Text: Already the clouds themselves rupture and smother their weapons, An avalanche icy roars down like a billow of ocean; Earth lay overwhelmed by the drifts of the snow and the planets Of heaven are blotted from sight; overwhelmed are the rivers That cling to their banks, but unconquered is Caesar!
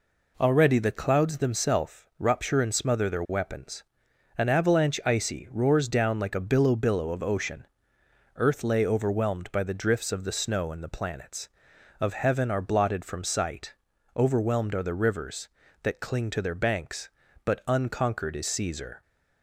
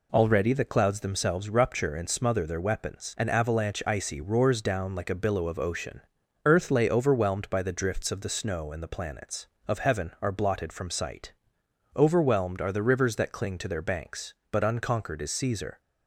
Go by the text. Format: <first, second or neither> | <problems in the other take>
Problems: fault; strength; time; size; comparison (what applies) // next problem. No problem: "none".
second | pauses between "themselves" and "rupture"; slight; at 2.0 s; 0.16 s long // says "billow" twice; at 6.7 s